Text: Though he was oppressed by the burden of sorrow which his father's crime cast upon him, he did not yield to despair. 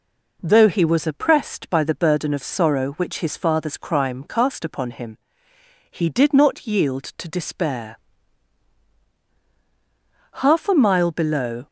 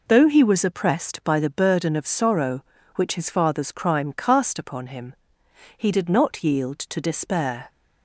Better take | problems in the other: second | goes on to say "Half a mile below"; noticeable; from 10.3 s on; 1.2 s long

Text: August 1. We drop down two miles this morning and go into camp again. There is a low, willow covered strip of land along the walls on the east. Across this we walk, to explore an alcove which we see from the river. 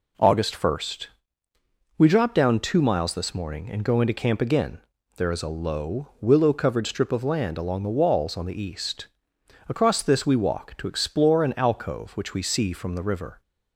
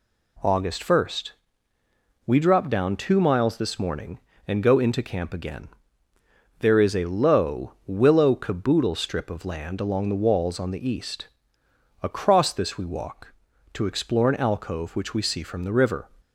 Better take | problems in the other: first | says "caboodle" for "covered"; at 8.3 s

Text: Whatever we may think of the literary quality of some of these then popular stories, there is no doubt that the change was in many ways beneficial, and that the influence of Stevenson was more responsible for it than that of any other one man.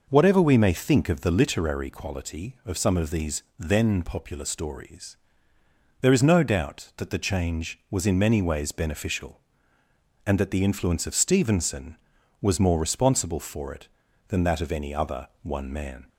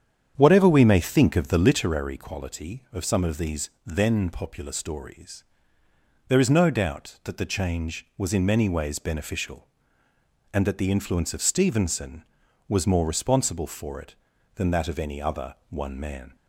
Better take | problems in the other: first | starts louder than the rest; strong; until 2.1 s; 8.5 dB // pauses between "these" and "then"; slight; at 3.6 s; 0.16 s long; slight in the first

